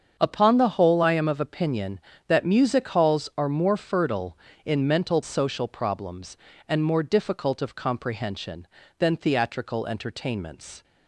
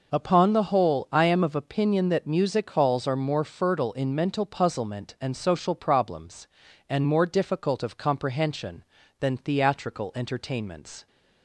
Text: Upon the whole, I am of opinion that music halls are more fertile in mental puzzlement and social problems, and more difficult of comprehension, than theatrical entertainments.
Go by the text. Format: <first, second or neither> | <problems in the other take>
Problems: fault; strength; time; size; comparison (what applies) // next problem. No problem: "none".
second | starts louder than the rest; strong; until 1.2 s; 7 dB // skips "puzzlement and"; at 5.2 s